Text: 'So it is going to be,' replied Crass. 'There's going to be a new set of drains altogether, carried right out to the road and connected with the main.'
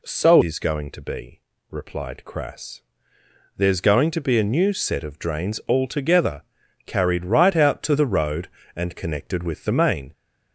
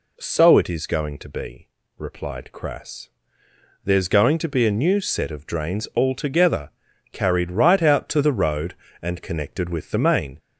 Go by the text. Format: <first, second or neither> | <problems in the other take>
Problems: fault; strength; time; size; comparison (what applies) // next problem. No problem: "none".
second | skips "it"; at 0.4 s